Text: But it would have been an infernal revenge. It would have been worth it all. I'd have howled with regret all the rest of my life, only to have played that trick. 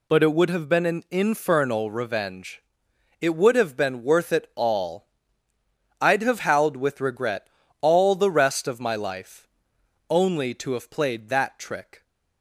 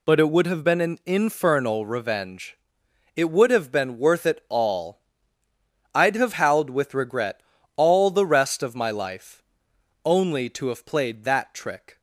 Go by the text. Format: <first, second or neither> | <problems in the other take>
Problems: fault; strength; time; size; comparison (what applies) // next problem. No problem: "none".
neither | pauses between "regret" and "all"; slight; the same in both